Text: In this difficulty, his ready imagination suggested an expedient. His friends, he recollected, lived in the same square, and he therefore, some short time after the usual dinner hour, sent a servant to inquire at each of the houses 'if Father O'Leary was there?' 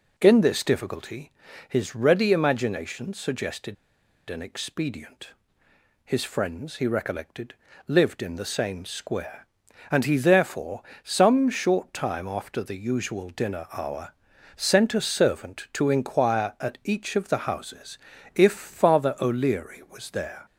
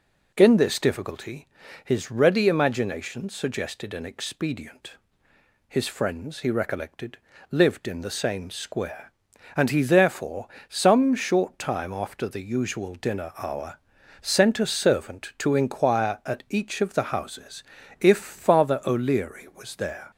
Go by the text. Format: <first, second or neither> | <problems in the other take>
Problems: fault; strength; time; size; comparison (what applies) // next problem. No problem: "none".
second | pauses between "suggested" and "an"; noticeable; at 3.7 s; 0.53 s long // pauses between "houses" and "if"; at 17.9 s; 0.38 s long; also in the second